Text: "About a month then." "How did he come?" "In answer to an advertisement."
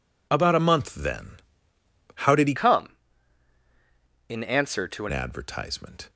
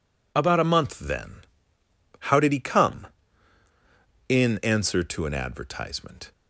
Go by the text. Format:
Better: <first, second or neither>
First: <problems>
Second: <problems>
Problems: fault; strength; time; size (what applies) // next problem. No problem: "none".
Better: second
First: changes voice from "come" to "an"; from 2.5 to 5.1 s; 2.6 s long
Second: none